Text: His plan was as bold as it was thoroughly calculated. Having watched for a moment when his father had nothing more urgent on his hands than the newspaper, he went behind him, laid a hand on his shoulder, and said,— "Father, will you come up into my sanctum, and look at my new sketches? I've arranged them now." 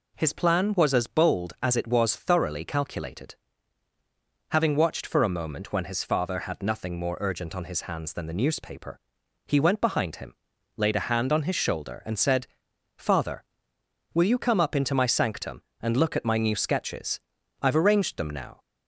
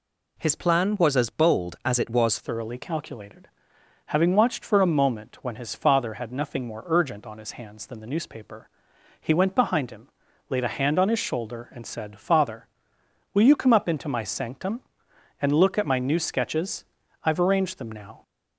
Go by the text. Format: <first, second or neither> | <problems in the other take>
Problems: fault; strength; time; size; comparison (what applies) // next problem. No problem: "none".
first | changes voice at "thoroughly"; from 2.3 s on; 15.9 s long